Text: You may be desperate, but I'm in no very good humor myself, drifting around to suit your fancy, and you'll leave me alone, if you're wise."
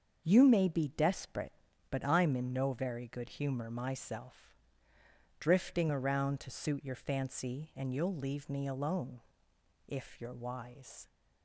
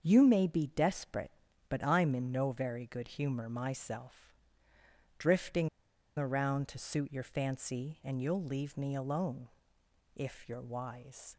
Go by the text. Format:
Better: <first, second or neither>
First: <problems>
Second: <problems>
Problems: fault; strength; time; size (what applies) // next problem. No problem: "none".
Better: first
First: starts louder than the rest; until 1.2 s; 7 dB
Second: starts louder than the rest; until 1.0 s; 7 dB // pauses between "drifting" and "around"; noticeable; at 5.6 s; 0.50 s long